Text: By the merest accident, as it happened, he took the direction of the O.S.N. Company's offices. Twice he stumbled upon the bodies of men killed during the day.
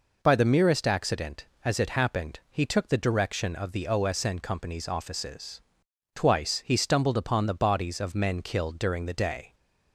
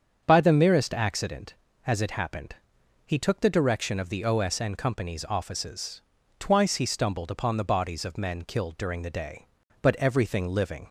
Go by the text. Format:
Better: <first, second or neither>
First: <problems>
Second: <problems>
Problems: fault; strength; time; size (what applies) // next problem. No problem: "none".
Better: first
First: none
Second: starts louder than the rest; strong; until 1.2 s; 7.5 dB // goes on to say "But everything living"; noticeable; from 9.8 s on; 1.0 s long